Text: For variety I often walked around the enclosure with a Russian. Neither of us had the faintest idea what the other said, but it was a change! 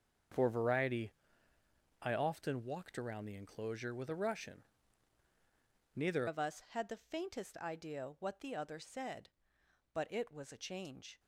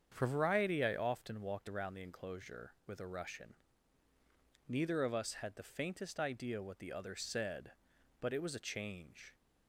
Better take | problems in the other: second | starts louder than the rest; until 2.2 s; 6.5 dB; strong in the second // pauses between "variety" and "I"; noticeable; at 1.1 s; 0.88 s long // changes voice at "of"; from 6.2 s on; 4.9 s long

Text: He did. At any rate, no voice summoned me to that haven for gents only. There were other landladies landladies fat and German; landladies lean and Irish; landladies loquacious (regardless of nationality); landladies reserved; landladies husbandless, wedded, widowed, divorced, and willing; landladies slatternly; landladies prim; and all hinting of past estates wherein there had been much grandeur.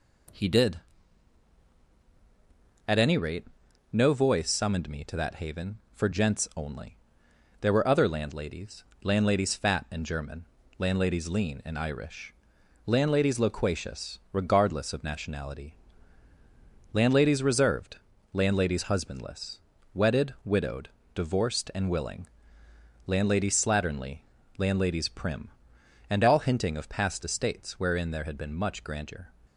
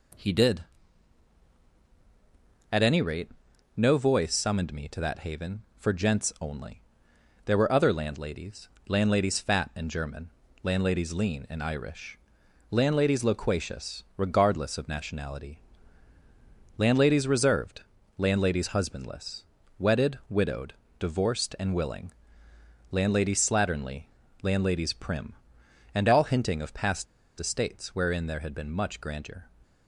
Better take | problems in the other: first | pauses between "landladies" and "landladies"; slight; at 8.6 s; 0.20 s long; slight in the first // pauses between "past" and "estates"; slight; at 27.0 s; 0.34 s long

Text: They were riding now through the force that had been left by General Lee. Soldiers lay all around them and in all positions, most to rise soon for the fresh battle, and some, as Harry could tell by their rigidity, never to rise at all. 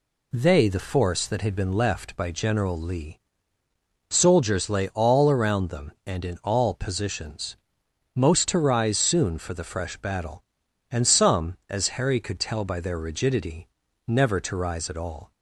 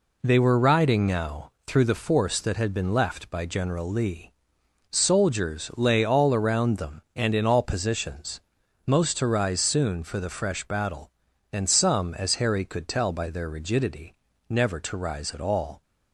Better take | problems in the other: second | skips "were riding now through"; at 0.6 s

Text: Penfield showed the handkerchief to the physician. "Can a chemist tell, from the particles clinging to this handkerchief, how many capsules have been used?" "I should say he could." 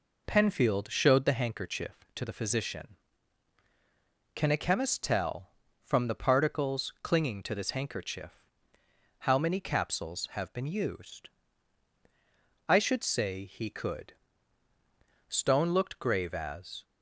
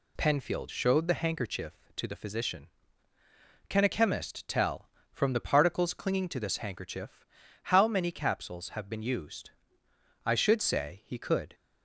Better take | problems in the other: second | goes on to say "Stone looked grave as"; from 15.2 s on; 1.5 s long

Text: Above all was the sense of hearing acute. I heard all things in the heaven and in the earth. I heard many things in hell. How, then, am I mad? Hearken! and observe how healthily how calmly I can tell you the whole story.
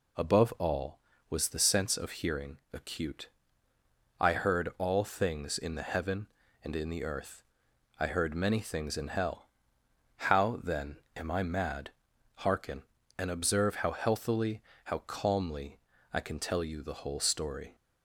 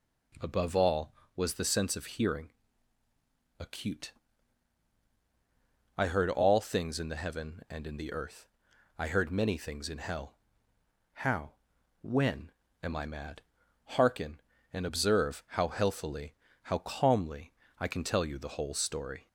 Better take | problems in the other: first | pauses between "hearing" and "acute"; at 2.5 s; 1.0 s long; slight in the first // says "when" for "then"; at 12.0 s // pauses between "healthily" and "how"; slight; at 16.3 s; 0.30 s long; slight in the first // pauses between "calmly" and "I"; slight; at 17.5 s; 0.26 s long; slight in the first

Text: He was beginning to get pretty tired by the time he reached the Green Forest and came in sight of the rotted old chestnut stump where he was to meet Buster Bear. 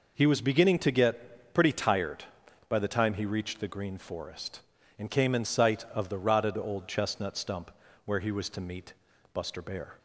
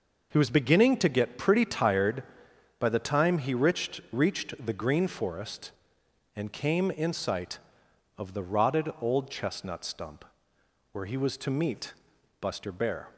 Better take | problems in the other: first | says "reached" twice; at 4.1 s // pauses between "stump" and "where"; noticeable; at 10.2 s; 0.70 s long; slight in the first // pauses between "meet" and "Buster"; noticeable; at 11.9 s; 0.48 s long; also in the first

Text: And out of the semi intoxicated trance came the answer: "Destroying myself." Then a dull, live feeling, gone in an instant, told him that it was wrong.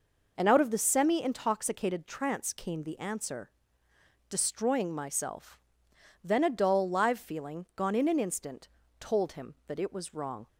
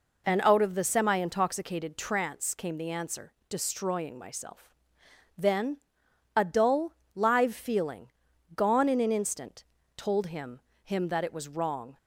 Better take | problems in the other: first | pauses between "Then" and "a"; noticeable; at 5.7 s; 0.58 s long // says "him" twice; at 10.8 s

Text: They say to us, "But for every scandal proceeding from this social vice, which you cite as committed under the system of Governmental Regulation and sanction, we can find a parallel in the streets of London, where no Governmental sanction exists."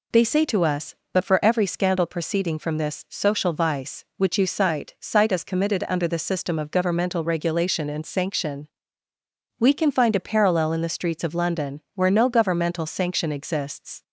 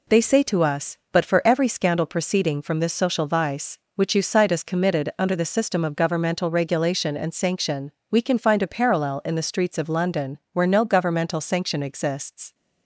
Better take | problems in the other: second | says "cite" twice; at 4.9 s

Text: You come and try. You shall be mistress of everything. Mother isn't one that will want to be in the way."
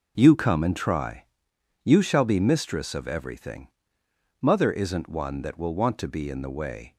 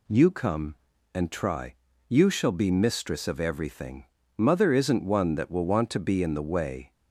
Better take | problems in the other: neither | none

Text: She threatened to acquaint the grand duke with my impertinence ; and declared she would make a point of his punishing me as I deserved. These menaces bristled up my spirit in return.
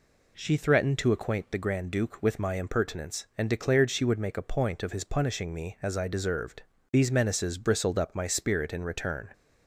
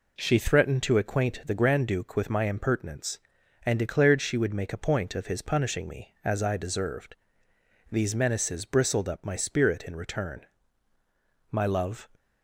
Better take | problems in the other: first | goes on to say "My love"; from 11.5 s on; 0.58 s long

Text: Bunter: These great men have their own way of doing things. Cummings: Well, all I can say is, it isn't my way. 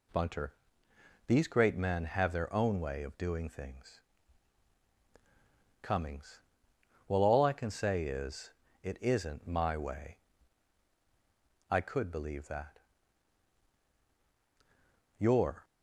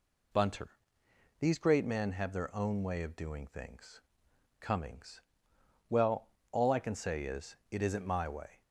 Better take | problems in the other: second | goes on to say "I could believe that your"; strong; from 11.6 s on; 3.9 s long

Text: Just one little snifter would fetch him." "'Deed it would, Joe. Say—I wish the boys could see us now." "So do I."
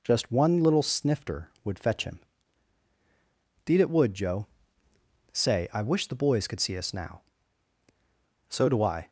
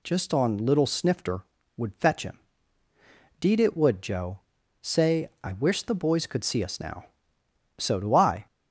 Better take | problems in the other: first | says "on" for "one"; at 0.3 s

